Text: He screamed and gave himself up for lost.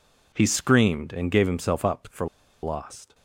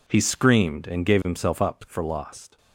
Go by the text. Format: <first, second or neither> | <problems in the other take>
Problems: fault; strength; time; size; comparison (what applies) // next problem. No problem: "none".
second | pauses between "for" and "lost"; at 2.2 s; 0.36 s long